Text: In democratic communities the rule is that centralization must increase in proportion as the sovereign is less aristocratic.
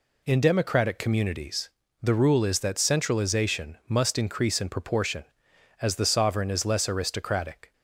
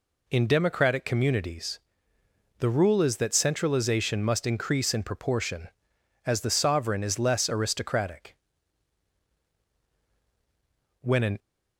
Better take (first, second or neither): first